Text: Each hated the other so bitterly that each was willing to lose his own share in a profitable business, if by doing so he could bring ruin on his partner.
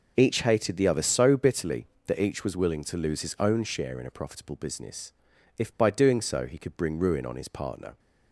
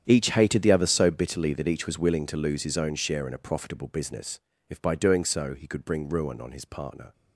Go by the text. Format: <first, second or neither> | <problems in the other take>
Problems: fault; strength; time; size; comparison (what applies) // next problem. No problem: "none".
first | gets quieter; strong; throughout; 15.5 dB